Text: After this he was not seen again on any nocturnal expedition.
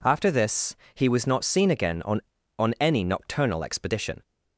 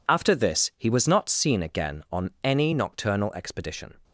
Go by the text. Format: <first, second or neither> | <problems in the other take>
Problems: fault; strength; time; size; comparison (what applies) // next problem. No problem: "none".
second | pauses between "this" and "he"; slight; at 0.7 s; 0.20 s long // says "on" twice; at 2.5 s